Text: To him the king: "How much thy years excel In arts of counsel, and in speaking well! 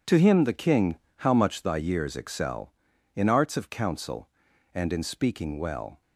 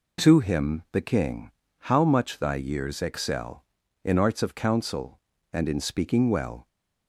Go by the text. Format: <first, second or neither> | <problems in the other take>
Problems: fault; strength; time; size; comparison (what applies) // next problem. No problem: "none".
neither | none